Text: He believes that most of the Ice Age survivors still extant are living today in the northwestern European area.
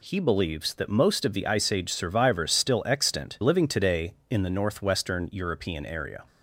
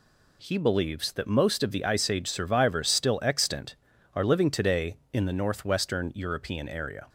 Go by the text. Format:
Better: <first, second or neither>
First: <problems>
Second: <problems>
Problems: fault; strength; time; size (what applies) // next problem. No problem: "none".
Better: second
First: skips "are"; at 3.3 s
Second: none